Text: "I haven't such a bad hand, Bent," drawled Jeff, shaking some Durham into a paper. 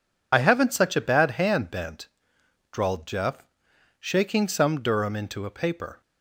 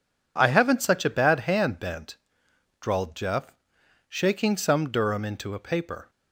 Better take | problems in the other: second | loses the start of "I"; at 0.3 s; 60 ms

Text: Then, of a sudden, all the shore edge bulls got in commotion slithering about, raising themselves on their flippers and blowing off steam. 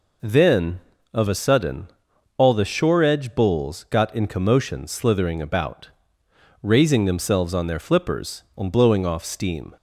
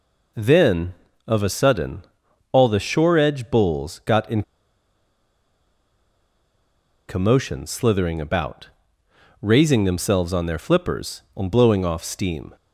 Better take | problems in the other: first | pauses between "in" and "commotion"; strong; at 4.4 s; 2.6 s long

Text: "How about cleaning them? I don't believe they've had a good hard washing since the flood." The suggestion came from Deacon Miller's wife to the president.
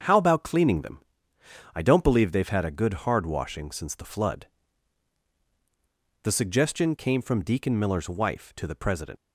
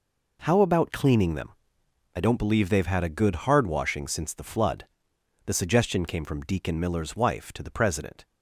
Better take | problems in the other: second | starts louder than the rest; until 1.7 s; 7 dB // leaves "president" unfinished; at 9.1 s; 85 ms

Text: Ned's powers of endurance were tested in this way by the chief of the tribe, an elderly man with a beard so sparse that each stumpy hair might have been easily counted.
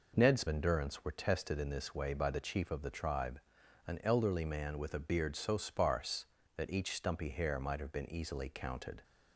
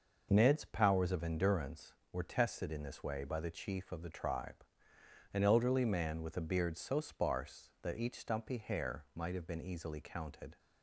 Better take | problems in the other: second | skips "powers of"; at 0.4 s

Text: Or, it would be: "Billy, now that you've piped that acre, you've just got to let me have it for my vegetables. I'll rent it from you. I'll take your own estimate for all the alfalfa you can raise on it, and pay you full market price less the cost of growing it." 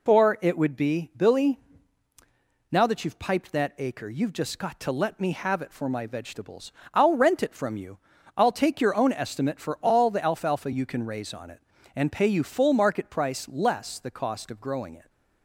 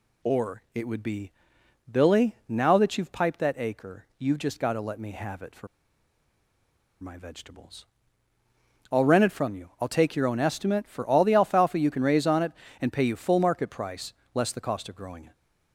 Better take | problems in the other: first | pauses between "for" and "my"; strong; at 5.6 s; 1.3 s long // pauses between "price" and "less"; slight; at 14.1 s; 0.20 s long

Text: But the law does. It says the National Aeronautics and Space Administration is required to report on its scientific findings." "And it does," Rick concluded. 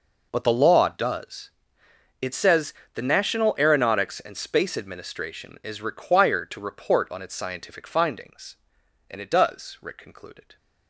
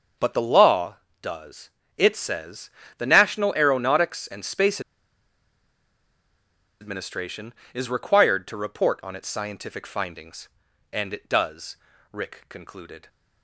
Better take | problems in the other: first | starts louder than the rest; until 1.4 s; 6.5 dB // pauses between "says" and "the"; slight; at 2.6 s; 0.28 s long; slight in the first // pauses between "Space" and "Administration"; strong; at 4.7 s; 2.0 s long

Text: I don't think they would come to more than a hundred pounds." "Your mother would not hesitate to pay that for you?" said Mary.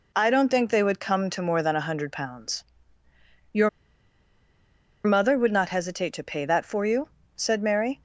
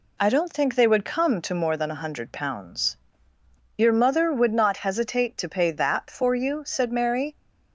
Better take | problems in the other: second | pauses between "Your" and "mother"; strong; at 3.6 s; 1.3 s long

